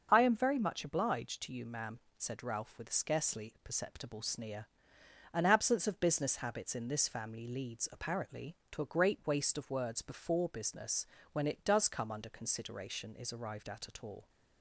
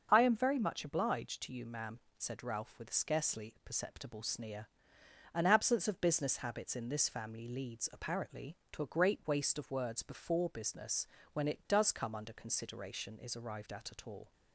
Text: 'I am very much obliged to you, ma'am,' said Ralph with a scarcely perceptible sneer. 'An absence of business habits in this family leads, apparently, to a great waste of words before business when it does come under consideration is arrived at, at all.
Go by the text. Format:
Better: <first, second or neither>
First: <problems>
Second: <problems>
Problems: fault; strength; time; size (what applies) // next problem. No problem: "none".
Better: neither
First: starts louder than the rest; until 1.1 s; 6 dB // pauses between "business" and "when"; slight; at 11.0 s; 0.28 s long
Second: starts louder than the rest; until 1.1 s; 6 dB // pauses between "business" and "when"; slight; at 11.0 s; 0.28 s long